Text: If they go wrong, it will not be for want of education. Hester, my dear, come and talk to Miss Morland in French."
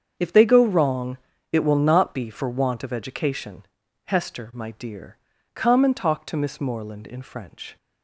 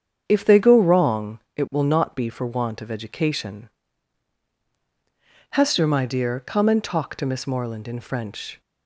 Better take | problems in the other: neither | starts louder than the rest; strong; the same in both

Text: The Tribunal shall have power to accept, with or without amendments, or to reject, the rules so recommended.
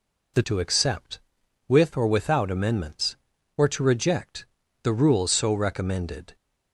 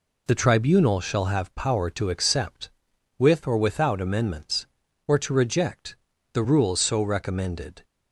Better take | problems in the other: second | skips "Tribunal shall have power"; at 0.4 s

